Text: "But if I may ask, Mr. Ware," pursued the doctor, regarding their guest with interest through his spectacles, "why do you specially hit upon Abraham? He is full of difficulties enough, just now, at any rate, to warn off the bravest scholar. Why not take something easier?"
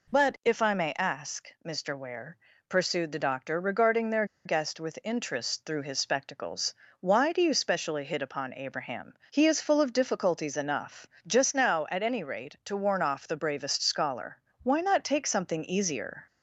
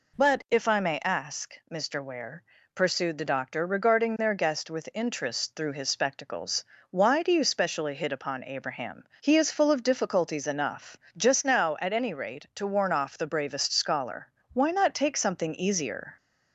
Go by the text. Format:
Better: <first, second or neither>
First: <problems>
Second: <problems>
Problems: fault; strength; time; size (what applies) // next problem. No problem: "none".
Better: second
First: pauses between "their" and "guest"; slight; at 4.2 s; 0.20 s long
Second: none